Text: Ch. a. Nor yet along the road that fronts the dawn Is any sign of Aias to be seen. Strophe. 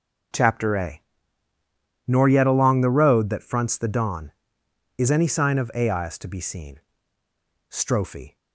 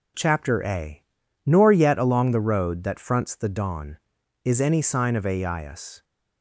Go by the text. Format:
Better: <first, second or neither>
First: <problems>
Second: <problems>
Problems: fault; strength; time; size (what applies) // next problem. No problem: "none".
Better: first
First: none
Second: stops before "to be seen Strophe"; at 6.0 s